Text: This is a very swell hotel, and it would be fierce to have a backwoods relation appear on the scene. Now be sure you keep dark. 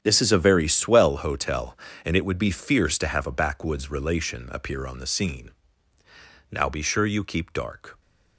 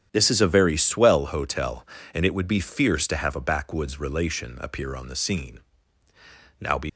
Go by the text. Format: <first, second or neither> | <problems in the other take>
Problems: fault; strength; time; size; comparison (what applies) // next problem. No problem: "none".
first | starts louder than the rest; strong; until 1.1 s; 9 dB; strong in the first // stops before "sure you keep dark"; at 6.8 s